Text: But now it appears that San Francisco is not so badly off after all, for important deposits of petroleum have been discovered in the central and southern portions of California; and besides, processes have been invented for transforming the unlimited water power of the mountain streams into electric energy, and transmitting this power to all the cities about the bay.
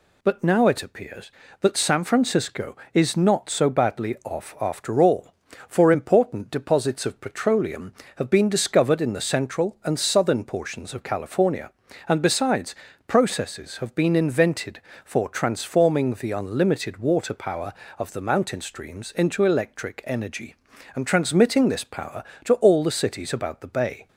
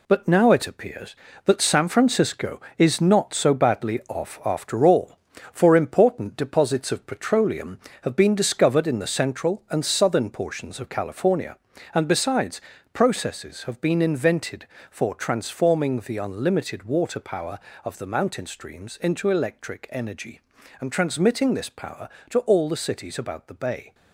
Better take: first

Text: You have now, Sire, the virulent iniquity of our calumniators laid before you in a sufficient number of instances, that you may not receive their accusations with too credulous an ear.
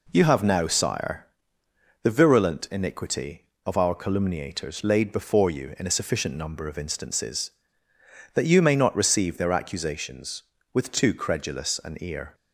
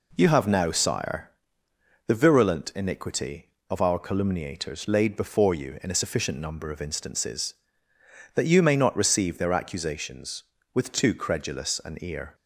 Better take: neither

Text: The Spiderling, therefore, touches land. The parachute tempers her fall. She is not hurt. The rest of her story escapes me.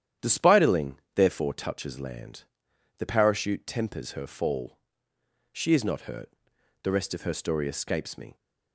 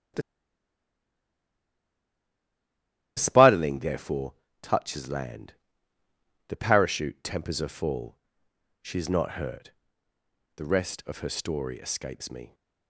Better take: first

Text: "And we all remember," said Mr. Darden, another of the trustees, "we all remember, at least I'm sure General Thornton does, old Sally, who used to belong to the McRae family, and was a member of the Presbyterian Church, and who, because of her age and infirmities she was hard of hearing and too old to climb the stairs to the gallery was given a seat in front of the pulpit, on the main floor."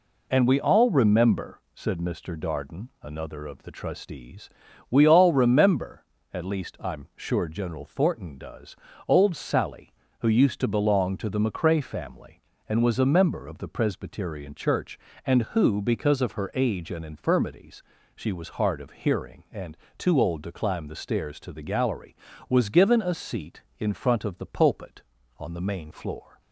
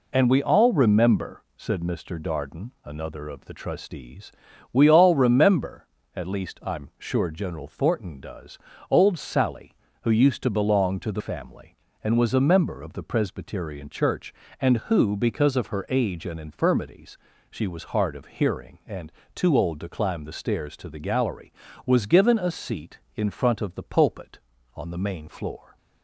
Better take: first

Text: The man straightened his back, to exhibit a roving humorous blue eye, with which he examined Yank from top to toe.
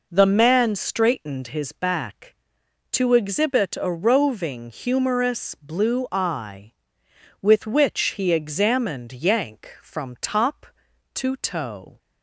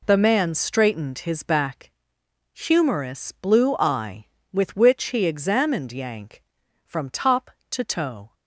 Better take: first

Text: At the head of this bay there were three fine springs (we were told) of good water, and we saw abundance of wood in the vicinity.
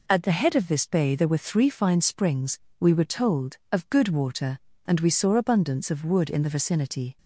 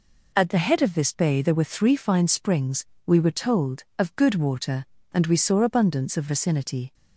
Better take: first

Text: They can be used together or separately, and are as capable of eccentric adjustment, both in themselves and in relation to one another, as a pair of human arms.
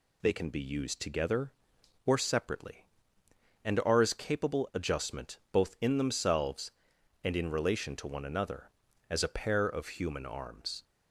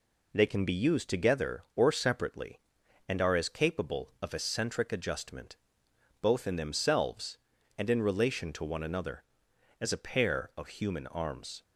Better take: second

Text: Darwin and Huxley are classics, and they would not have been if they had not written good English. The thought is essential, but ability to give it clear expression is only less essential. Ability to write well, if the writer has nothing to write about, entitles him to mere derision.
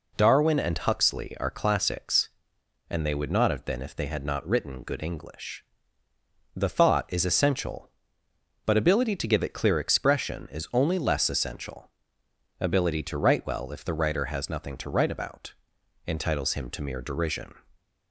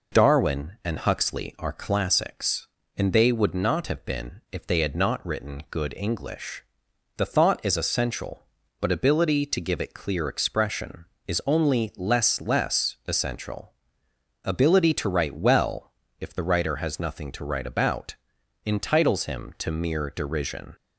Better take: first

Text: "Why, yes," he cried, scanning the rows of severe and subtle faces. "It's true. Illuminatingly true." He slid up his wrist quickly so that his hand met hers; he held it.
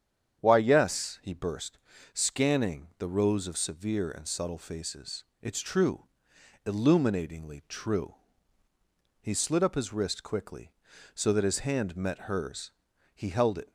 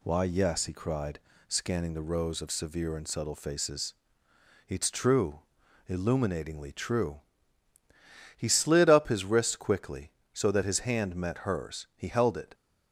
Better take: second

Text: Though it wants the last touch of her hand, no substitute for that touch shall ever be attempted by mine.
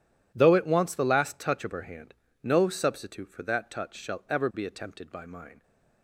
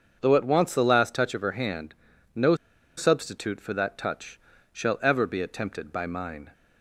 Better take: first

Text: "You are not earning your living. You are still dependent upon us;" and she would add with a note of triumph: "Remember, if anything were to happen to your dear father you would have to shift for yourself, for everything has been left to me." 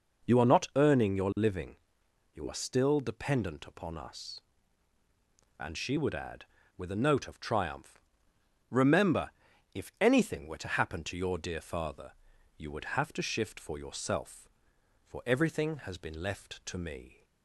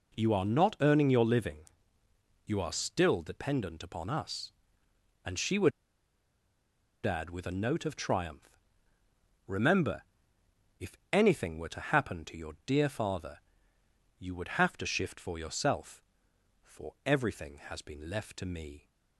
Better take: first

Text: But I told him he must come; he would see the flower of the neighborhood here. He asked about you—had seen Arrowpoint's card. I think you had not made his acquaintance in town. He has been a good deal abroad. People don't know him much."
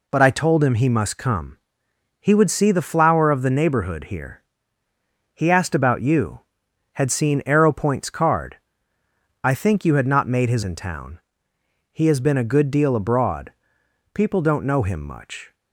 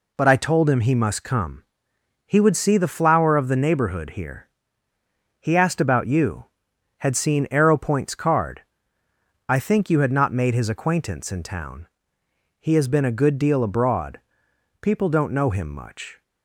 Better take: second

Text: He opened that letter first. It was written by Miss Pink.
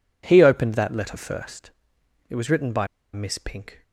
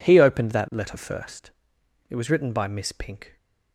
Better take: second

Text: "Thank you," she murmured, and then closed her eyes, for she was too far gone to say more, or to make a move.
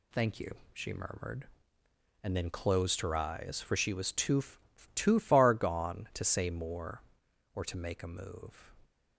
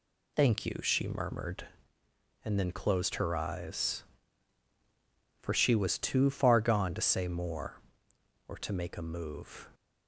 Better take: second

